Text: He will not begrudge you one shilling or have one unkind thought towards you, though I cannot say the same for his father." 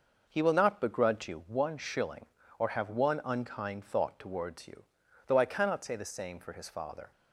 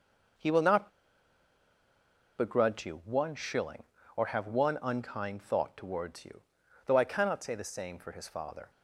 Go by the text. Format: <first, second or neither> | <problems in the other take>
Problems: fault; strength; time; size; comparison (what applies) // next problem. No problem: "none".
first | pauses between "not" and "begrudge"; strong; at 0.8 s; 1.4 s long